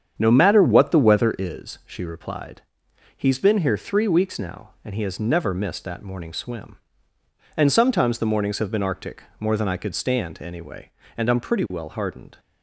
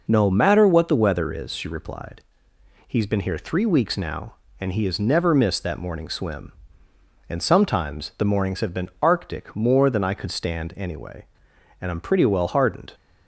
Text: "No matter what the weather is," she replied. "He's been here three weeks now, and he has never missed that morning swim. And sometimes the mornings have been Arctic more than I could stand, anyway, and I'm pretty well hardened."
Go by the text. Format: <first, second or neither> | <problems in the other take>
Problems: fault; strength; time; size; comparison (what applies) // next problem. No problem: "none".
second | starts louder than the rest; strong; until 1.5 s; 8 dB // pauses between "Arctic" and "more"; slight; at 9.2 s; 0.18 s long